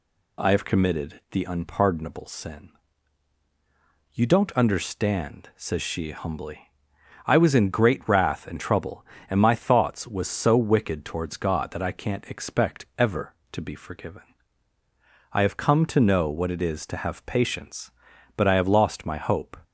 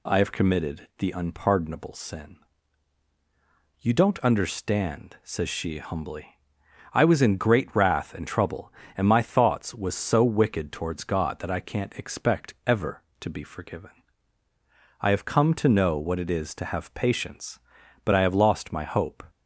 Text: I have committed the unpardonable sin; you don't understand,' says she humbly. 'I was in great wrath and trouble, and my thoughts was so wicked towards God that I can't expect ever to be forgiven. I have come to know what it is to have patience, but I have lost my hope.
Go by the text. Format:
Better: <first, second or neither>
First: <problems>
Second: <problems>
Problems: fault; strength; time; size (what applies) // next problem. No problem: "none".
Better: neither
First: none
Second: none